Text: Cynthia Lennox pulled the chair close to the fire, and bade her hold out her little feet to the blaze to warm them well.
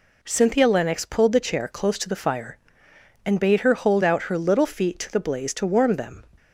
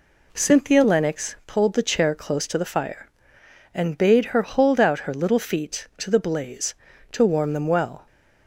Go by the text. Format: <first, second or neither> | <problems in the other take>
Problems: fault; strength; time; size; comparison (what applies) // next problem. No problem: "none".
second | stops before "well"; at 6.3 s